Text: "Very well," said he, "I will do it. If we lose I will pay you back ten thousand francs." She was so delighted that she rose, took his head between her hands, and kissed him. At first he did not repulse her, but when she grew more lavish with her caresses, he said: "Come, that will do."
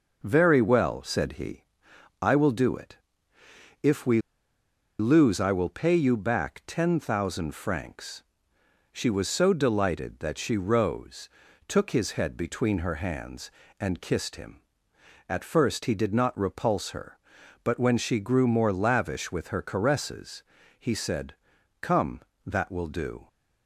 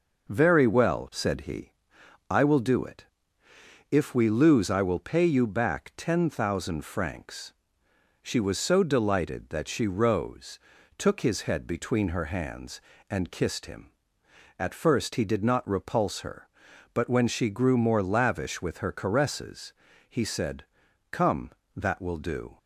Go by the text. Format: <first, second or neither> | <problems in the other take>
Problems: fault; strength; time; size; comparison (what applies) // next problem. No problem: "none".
second | pauses between "we" and "lose"; noticeable; at 4.2 s; 0.78 s long